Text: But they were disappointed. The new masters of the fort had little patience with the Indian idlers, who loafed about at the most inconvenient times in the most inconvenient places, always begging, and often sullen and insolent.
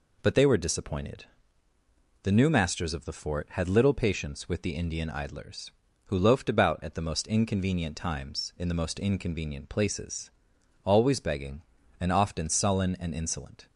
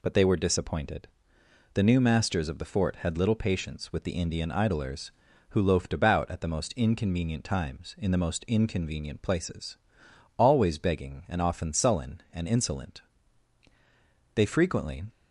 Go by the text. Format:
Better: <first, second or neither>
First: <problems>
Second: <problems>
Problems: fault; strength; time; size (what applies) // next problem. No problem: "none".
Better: first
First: none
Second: goes on to say "They frequently"; noticeable; from 14.3 s on; 0.70 s long